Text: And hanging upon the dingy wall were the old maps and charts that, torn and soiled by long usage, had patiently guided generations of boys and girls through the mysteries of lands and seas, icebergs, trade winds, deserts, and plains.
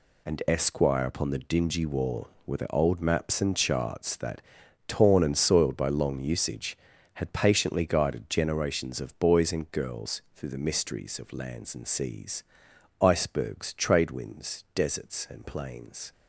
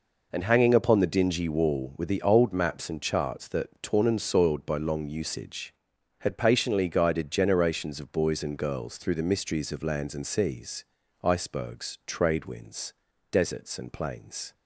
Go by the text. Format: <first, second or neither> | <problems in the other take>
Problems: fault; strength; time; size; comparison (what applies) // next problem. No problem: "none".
second | says "esquire" for "hanging"; at 0.4 s